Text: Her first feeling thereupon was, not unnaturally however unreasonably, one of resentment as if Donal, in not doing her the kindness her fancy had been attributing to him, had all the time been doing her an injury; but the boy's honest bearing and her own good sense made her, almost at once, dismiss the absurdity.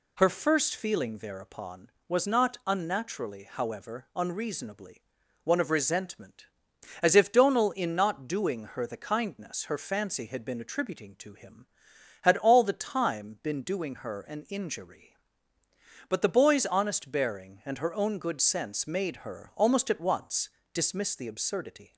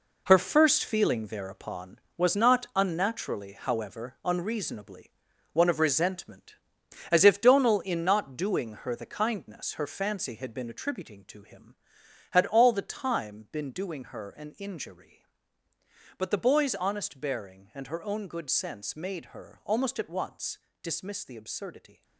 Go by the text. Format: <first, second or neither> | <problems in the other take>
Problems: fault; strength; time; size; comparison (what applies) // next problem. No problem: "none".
first | gets quieter; strong; throughout; 9 dB